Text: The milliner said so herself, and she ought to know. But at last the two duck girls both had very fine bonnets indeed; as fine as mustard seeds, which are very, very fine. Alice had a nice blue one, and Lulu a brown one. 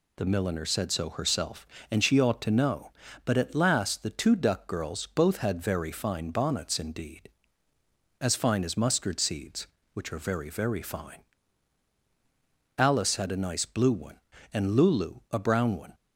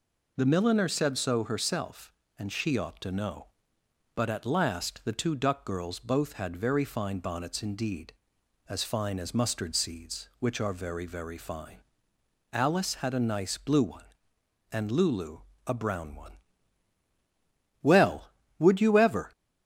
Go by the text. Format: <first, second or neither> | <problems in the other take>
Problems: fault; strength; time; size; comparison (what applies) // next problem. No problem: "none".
first | pauses between "Lulu" and "a"; slight; at 15.3 s; 0.28 s long // goes on to say "Well would you ever"; from 17.8 s on; 1.5 s long